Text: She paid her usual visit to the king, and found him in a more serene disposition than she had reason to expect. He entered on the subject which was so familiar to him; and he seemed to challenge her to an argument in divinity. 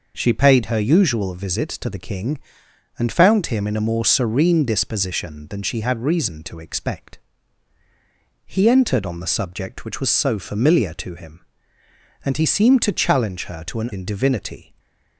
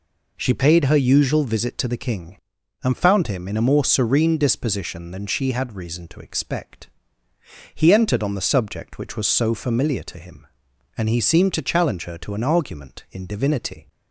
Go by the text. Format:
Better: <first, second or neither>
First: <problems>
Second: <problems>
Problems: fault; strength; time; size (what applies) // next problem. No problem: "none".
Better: second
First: skips "argument"; at 13.9 s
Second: none